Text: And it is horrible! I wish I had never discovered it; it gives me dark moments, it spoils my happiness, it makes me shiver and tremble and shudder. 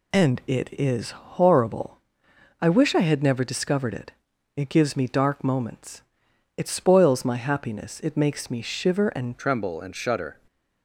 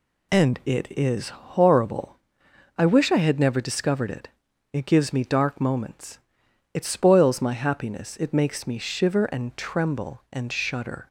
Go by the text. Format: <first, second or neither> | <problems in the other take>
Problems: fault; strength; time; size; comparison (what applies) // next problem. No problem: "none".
second | changes voice at "tremble"; from 9.3 s on; 1.0 s long // stays silent after the last word; slight; from 10.3 s on; 0.5 s long